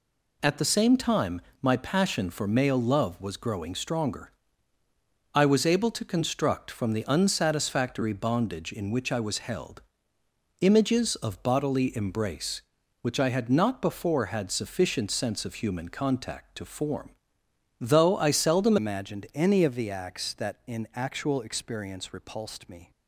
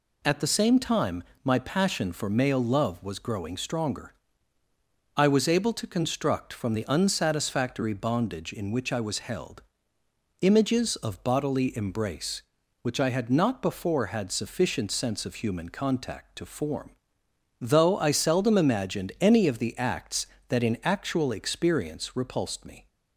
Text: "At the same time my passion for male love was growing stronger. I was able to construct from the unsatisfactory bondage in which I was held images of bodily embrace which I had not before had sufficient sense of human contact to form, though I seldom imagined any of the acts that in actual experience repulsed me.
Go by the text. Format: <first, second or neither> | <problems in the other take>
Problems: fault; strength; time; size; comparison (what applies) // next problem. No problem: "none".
second | pauses between "time" and "my"; slight; at 1.4 s; 0.20 s long; slight in the second // pauses between "held" and "images"; noticeable; at 9.8 s; 0.78 s long; noticeable in the second // changes voice at "imagined"; from 18.7 s on; 4.2 s long